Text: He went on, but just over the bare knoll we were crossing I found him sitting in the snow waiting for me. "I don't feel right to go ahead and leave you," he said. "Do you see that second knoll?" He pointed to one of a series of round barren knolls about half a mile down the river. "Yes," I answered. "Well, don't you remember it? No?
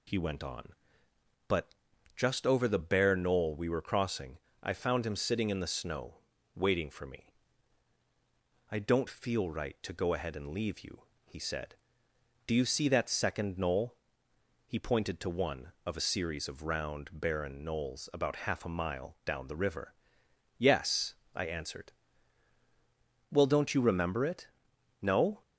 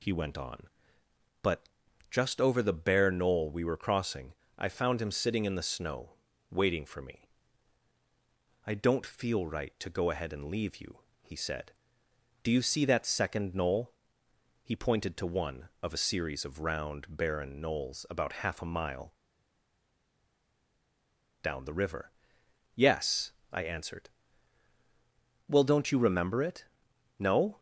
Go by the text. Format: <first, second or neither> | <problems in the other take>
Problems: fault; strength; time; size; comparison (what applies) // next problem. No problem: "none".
first | pauses between "but" and "just"; at 1.6 s; 0.42 s long; also in the first // pauses between "crossing" and "I"; slight; at 4.3 s; 0.26 s long; slight in the first // pauses between "snow" and "waiting"; slight; at 6.1 s; 0.36 s long; slight in the first // pauses between "mile" and "down"; strong; at 19.1 s; 2.3 s long